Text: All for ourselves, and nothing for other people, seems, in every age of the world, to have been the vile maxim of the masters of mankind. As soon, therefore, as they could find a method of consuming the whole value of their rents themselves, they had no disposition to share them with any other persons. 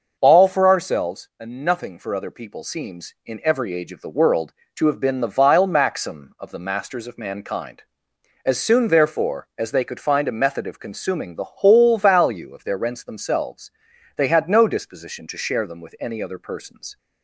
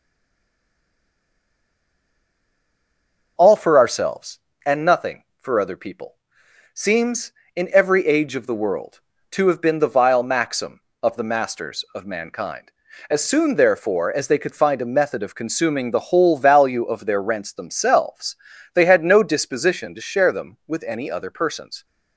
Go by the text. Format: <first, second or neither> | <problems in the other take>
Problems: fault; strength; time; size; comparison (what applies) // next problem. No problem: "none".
first | stays silent before the first word; strong; until 3.3 s; 3.3 s long